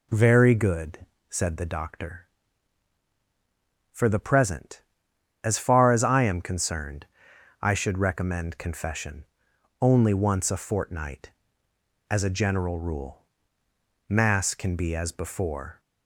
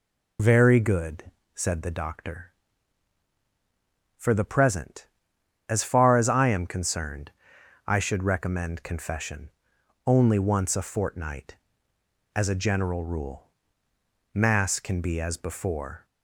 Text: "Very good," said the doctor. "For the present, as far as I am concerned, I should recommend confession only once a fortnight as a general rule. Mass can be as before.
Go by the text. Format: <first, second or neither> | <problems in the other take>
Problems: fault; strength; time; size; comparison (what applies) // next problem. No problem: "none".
first | loses the start of "Very"; at 0.3 s; 50 ms // pauses between "confession" and "only"; noticeable; at 9.5 s; 0.54 s long; noticeable in the first